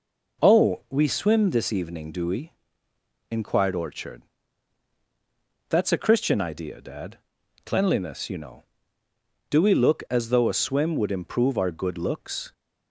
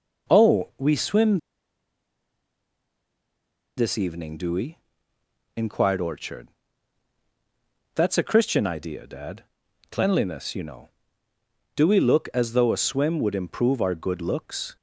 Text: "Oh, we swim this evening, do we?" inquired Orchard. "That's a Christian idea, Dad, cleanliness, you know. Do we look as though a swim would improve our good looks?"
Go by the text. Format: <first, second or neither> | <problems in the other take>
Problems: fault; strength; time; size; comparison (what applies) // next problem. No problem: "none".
first | pauses between "swim" and "this"; strong; at 1.3 s; 2.3 s long